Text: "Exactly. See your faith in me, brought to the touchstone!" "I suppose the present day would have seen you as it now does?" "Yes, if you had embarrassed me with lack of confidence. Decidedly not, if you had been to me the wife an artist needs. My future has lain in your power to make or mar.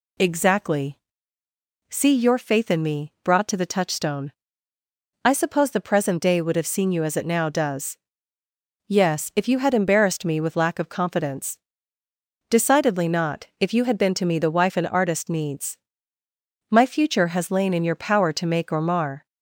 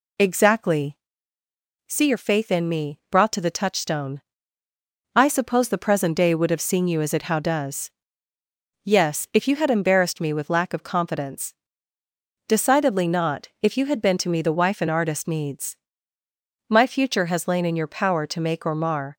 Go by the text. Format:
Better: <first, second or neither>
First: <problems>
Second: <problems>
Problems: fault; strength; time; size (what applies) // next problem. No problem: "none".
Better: first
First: none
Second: says "how" for "now"; at 7.2 s